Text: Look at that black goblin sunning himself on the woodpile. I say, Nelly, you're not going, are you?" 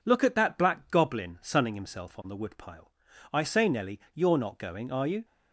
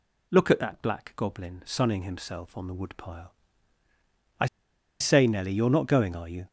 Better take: first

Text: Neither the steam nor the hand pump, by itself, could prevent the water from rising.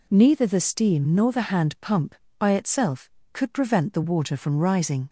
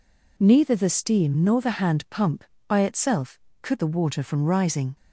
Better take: first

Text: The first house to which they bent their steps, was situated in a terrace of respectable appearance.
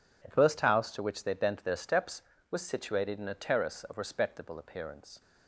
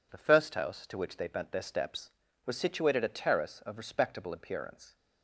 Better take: first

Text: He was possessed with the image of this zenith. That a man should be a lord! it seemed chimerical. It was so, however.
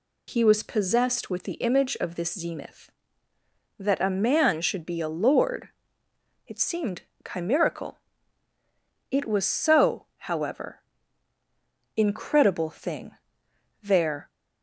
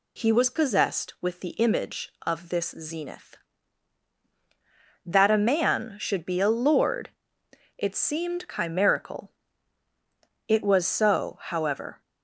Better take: second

